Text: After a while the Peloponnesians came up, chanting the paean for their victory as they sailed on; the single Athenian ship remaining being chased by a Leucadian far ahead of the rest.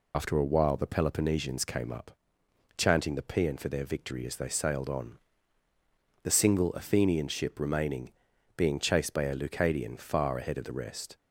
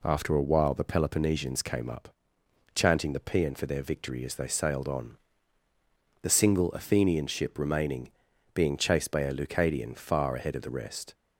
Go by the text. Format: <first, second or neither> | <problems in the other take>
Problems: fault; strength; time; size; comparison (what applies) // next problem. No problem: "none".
second | loses the start of "After"; at 0.1 s; 105 ms // pauses between "remaining" and "being"; noticeable; at 8.1 s; 0.46 s long; also in the second